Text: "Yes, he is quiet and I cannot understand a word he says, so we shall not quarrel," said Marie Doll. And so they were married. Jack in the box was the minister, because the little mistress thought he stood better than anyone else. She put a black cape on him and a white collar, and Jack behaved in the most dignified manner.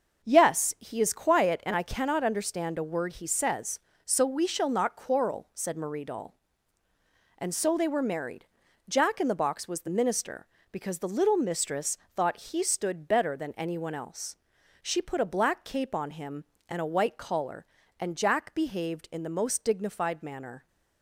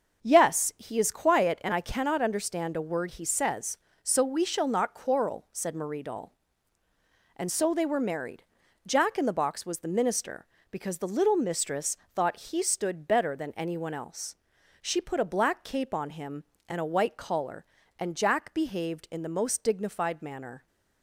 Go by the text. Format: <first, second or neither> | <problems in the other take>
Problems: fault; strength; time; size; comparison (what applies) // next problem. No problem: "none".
neither | starts louder than the rest; the same in both // pauses between "mistress" and "thought"; slight; the same in both